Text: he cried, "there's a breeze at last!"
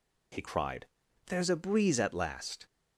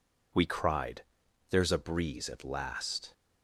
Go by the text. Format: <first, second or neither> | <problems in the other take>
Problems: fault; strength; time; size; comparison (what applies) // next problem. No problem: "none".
first | says "we" for "he"; at 0.3 s